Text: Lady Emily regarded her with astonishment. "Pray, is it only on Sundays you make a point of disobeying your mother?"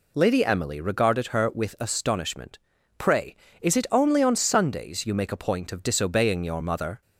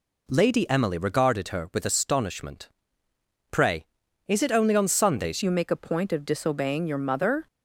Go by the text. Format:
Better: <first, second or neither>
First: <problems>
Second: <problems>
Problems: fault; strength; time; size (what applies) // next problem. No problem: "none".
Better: first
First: none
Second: changes voice at "you"; from 5.4 s on; 2.0 s long